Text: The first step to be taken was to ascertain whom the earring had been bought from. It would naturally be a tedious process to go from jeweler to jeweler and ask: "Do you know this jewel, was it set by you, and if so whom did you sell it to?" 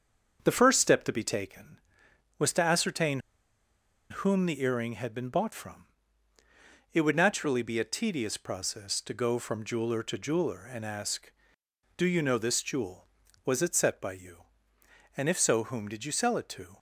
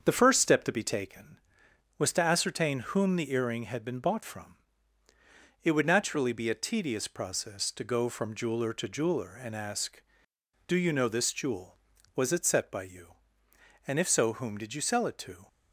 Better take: second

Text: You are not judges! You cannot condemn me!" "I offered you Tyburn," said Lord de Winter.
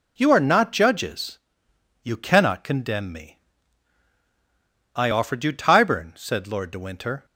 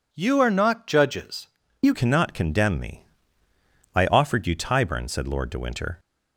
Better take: first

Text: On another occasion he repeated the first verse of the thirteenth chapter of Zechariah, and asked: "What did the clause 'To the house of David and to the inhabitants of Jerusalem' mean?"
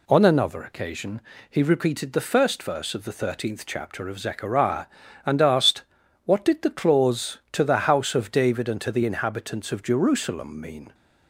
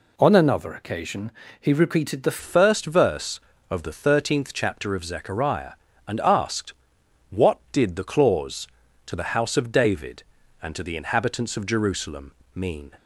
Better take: first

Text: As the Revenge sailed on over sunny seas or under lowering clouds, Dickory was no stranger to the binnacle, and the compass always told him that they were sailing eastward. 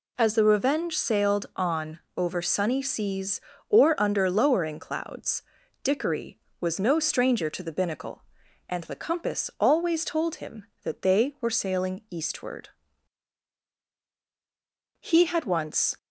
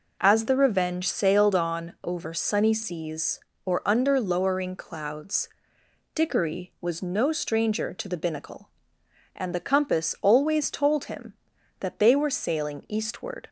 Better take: second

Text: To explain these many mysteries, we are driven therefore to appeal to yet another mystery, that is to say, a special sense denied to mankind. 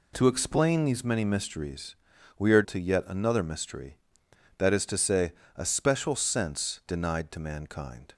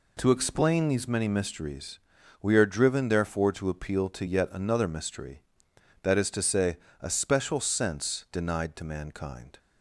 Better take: second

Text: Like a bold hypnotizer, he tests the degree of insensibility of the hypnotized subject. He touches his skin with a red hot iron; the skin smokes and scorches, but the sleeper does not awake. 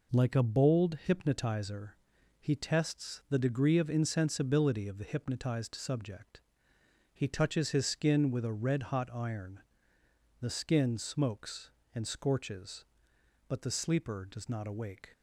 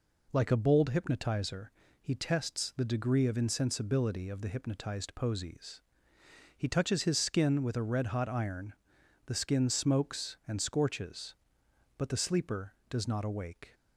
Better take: first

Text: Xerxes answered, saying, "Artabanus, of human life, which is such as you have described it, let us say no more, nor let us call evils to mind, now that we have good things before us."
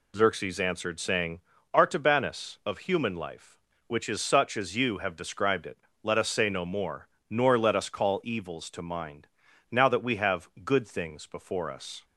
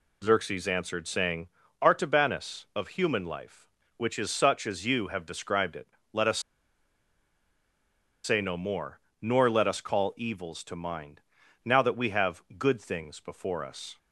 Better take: first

